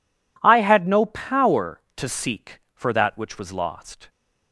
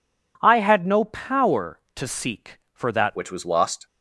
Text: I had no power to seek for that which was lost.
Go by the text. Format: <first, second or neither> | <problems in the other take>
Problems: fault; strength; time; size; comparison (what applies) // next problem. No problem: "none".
first | changes voice at "which"; from 3.1 s on; 0.7 s long